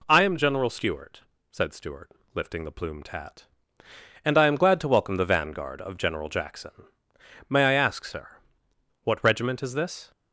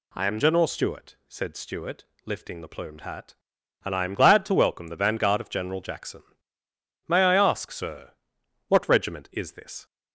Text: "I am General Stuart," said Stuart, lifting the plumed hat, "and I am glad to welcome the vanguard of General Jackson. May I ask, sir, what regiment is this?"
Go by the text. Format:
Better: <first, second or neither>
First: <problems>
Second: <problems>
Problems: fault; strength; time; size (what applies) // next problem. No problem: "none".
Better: neither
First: none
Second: none